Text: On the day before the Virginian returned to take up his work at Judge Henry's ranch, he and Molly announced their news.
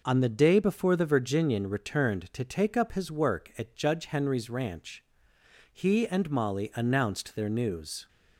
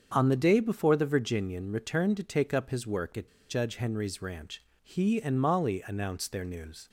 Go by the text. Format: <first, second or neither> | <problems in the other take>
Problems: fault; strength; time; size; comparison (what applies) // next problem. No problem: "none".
first | starts louder than the rest; strong; until 1.1 s; 7 dB // pauses between "at" and "Judge"; slight; at 3.2 s; 0.20 s long